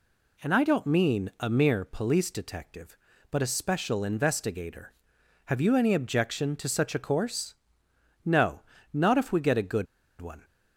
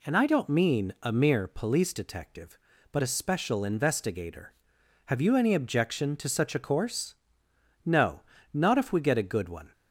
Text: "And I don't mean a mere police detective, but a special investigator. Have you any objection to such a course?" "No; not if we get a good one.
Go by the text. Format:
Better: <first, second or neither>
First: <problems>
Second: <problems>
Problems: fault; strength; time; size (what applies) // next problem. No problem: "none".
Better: second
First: pauses between "good" and "one"; slight; at 9.8 s; 0.34 s long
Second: none